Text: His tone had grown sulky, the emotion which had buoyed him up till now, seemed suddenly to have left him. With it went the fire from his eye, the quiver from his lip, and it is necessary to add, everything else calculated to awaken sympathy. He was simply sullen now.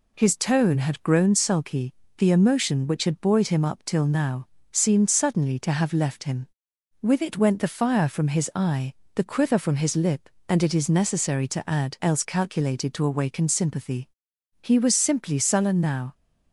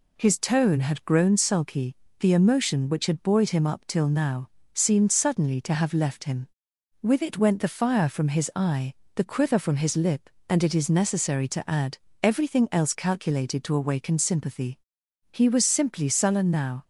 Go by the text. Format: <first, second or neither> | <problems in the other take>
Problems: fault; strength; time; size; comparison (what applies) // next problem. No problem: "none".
second | skips "everything"; at 11.9 s